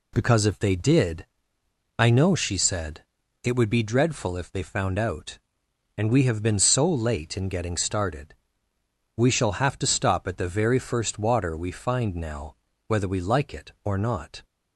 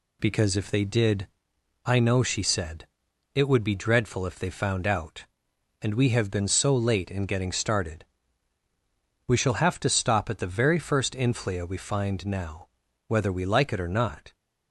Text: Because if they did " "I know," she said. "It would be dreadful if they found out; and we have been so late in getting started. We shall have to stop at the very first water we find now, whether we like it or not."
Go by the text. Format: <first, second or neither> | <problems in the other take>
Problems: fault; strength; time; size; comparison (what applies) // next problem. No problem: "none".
first | says "inflia" for "water"; at 11.1 s